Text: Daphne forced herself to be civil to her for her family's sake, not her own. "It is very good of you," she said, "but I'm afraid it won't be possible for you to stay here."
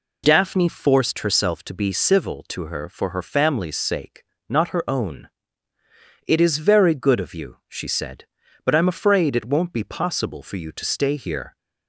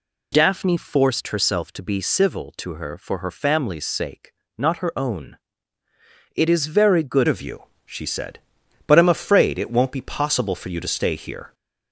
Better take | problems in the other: first | changes voice at "of"; from 7.2 s on; 4.3 s long

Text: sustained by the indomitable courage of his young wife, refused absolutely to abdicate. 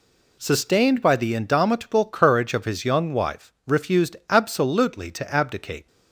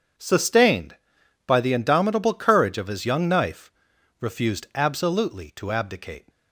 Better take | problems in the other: first | says "knife" for "wife"; at 3.2 s

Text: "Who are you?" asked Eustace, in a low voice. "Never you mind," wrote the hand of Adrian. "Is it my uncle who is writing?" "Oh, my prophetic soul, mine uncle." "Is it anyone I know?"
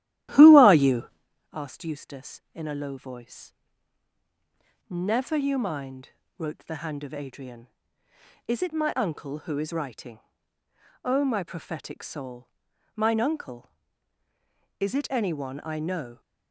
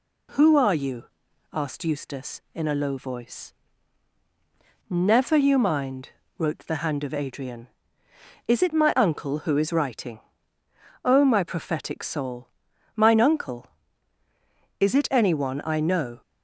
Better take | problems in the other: second | starts louder than the rest; strong; until 1.3 s; 13.5 dB

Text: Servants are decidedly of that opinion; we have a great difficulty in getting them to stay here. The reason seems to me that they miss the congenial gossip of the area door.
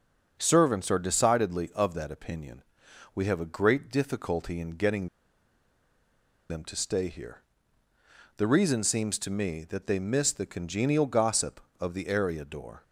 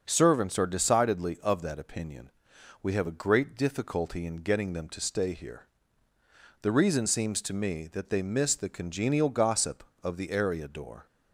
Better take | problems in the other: second | starts louder than the rest; until 1.4 s; 6 dB; also in the second // pauses between "getting" and "them"; strong; at 5.0 s; 1.4 s long

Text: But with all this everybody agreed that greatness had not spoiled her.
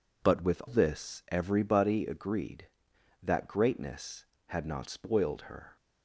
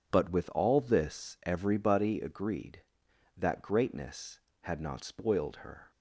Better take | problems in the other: second | skips "all"; at 0.6 s

